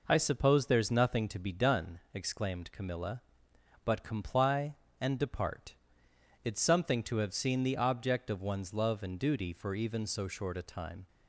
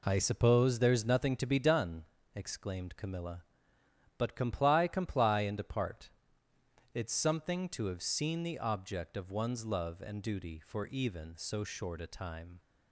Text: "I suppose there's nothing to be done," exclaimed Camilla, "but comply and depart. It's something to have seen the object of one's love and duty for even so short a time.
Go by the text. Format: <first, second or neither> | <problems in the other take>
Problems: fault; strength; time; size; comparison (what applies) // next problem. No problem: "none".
first | says "comply" twice; at 4.8 s